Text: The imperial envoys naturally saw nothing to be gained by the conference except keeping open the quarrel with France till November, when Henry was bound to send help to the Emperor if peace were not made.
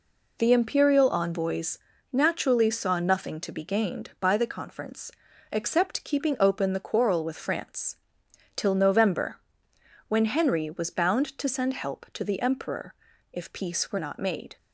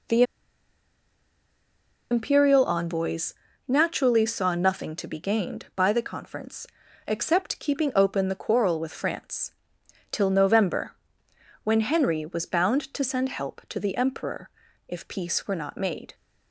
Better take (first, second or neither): first